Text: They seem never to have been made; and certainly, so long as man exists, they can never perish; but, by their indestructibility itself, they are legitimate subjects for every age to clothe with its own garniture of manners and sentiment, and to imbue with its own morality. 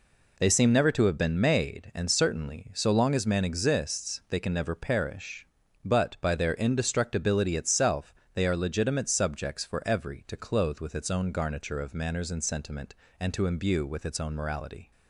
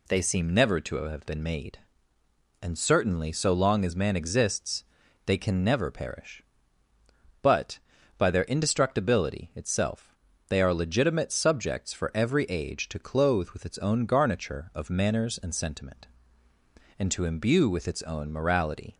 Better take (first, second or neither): second